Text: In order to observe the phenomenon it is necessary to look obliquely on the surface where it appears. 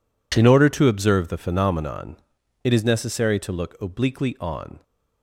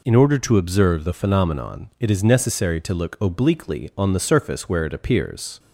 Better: second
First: pauses between "phenomenon" and "it"; noticeable; at 2.1 s; 0.46 s long // stops before "the surface where it appears"; at 4.8 s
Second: none

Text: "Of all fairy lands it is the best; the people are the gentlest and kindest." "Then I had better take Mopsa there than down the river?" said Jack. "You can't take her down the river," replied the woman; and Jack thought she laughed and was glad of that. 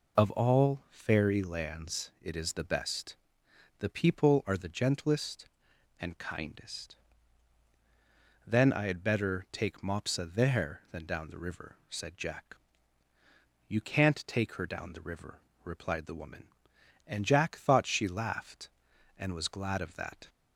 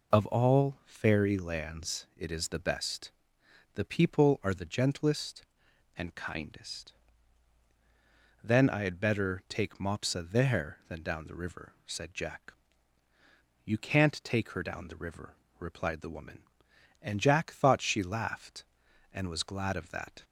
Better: neither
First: none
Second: none

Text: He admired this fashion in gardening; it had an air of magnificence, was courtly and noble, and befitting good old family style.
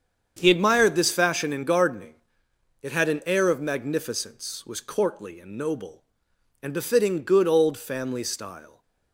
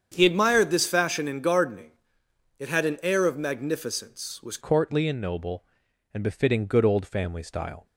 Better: first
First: starts louder than the rest; strong; until 1.4 s; 7.5 dB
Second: starts louder than the rest; strong; until 1.1 s; 8 dB // changes voice at "courtly"; from 4.6 s on; 3.2 s long

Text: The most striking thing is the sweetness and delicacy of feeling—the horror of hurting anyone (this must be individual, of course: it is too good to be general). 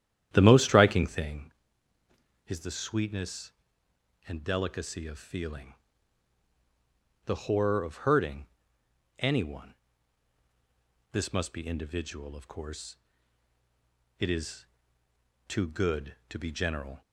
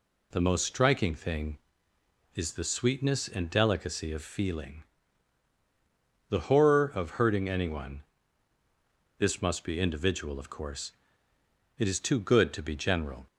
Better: second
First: starts louder than the rest; strong; until 1.5 s; 11 dB // pauses between "hurting" and "anyone"; noticeable; at 8.4 s; 0.72 s long // pauses between "is" and "too"; noticeable; at 14.6 s; 0.80 s long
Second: none

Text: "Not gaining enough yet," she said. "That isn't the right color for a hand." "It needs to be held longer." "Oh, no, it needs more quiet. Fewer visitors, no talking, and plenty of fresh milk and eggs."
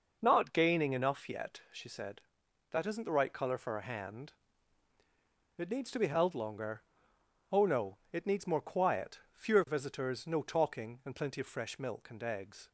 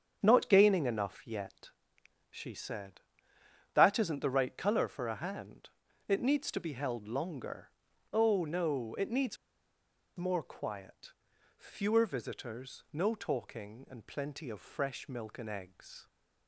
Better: first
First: none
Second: starts louder than the rest; strong; until 1.2 s; 7.5 dB // pauses between "needs" and "more"; noticeable; at 9.3 s; 0.81 s long

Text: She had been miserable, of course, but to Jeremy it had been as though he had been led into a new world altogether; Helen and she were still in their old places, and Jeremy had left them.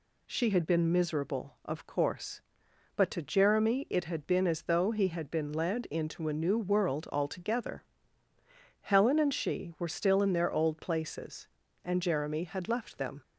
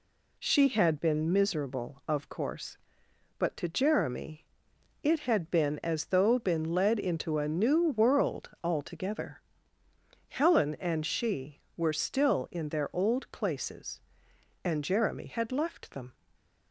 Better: first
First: none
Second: pauses between "Jeremy" and "it"; noticeable; at 4.4 s; 0.56 s long // skips "he had"; at 6.3 s

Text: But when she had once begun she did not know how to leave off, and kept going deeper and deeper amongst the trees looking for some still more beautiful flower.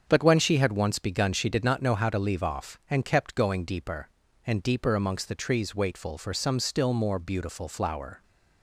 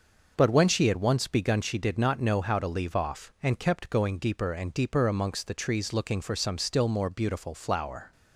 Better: second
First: starts louder than the rest; strong; until 1.0 s; 7.5 dB // says "waitful" for "looking"; at 5.7 s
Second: starts louder than the rest; until 1.3 s; 6.5 dB

